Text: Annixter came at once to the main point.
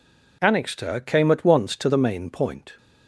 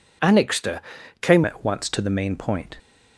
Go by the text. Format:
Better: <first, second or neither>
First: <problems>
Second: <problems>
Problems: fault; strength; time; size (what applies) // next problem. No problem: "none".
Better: first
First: none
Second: pauses between "Annixter" and "came"; at 0.8 s; 0.40 s long // changes voice at "at"; from 1.4 s on; 1.3 s long